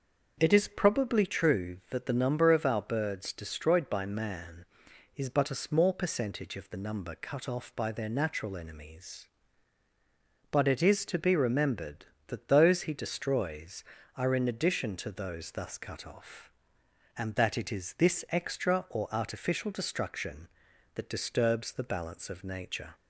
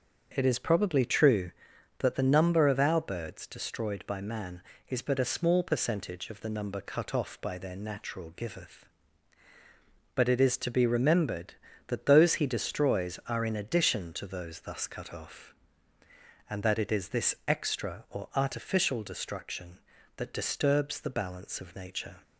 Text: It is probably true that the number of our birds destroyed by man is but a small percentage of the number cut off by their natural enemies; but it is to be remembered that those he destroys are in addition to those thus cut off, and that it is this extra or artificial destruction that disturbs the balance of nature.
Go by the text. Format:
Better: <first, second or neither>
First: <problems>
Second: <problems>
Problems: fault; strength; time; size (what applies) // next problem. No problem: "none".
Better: first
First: starts louder than the rest; until 1.4 s; 6.5 dB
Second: starts louder than the rest; until 1.3 s; 6.5 dB // says "giveth" for "enemies"; at 8.3 s